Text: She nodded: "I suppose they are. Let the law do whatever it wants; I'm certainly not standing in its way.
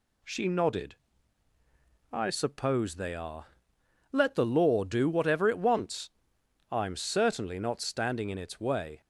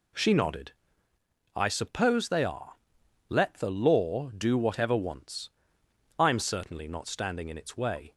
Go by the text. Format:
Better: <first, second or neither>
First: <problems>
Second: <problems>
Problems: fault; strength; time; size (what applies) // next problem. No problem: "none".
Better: first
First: none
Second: skips "it"; at 4.9 s